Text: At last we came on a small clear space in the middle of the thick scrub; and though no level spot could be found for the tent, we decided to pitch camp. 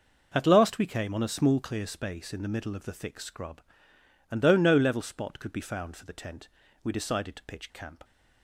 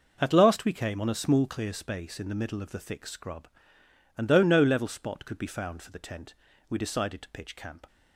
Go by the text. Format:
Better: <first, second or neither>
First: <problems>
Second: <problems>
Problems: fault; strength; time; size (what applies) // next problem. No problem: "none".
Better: neither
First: none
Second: none